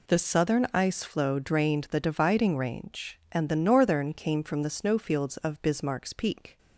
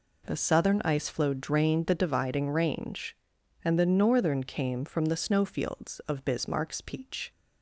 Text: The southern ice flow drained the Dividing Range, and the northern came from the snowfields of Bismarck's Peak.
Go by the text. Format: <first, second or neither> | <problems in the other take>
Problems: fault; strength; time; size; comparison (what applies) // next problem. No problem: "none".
first | says "Peach" for "Peak"; at 6.8 s